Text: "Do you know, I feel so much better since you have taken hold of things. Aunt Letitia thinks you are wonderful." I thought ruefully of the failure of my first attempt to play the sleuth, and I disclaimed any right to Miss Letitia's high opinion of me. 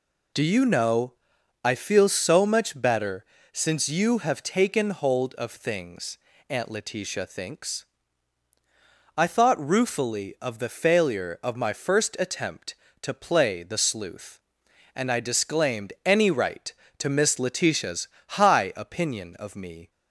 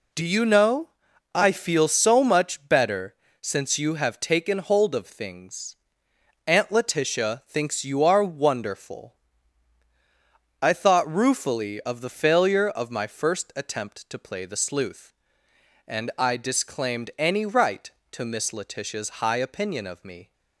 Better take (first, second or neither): second